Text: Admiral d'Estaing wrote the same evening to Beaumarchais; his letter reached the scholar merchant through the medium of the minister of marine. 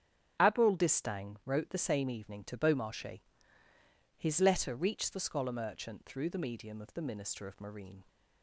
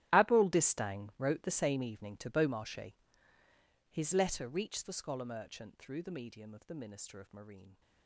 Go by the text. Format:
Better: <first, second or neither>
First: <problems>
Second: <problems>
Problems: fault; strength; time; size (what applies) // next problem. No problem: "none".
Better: first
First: starts louder than the rest; strong; until 1.4 s; 8 dB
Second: gets quieter; strong; throughout; 17 dB // starts louder than the rest; strong; until 1.2 s; 13 dB